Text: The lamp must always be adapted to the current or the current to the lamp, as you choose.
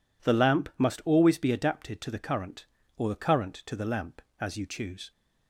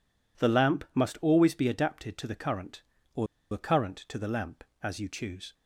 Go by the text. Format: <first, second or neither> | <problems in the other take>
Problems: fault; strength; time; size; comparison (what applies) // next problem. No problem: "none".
first | pauses between "or" and "the"; slight; at 3.2 s; 0.26 s long